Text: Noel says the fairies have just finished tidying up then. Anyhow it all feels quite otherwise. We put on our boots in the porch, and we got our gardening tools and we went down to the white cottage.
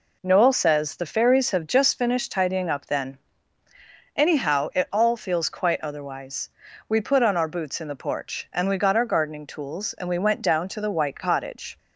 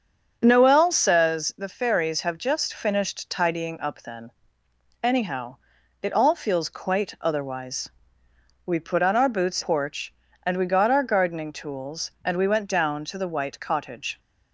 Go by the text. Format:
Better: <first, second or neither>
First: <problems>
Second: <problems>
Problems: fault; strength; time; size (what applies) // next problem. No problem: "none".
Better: first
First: none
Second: starts louder than the rest; until 1.4 s; 7 dB // pauses between "Anyhow" and "it"; at 5.5 s; 0.44 s long // skips "in the"; at 9.6 s